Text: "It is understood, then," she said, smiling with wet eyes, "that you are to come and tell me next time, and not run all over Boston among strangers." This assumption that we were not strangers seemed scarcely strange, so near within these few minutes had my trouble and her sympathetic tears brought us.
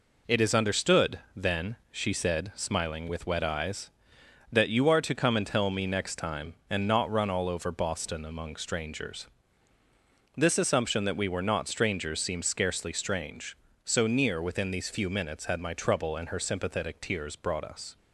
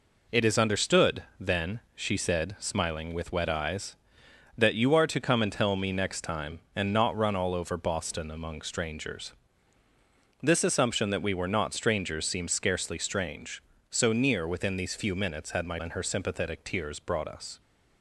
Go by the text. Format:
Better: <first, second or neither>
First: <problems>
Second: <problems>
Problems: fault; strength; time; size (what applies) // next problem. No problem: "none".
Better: first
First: none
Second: skips "trouble"; at 15.7 s